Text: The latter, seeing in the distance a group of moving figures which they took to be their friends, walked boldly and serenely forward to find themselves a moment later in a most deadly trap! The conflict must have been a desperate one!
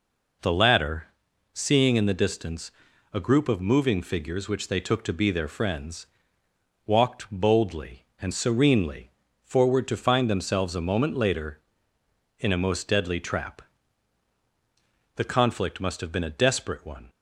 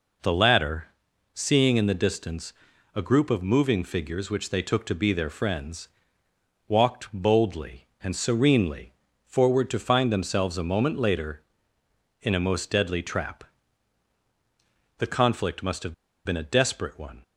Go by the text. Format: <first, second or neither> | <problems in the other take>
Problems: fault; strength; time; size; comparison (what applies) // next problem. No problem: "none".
first | pauses between "distance" and "a"; at 2.5 s; 0.42 s long; also in the first // pauses between "serenely" and "forward"; slight; at 8.9 s; 0.32 s long; slight in the first // pauses between "have" and "been"; slight; at 15.9 s; 0.31 s long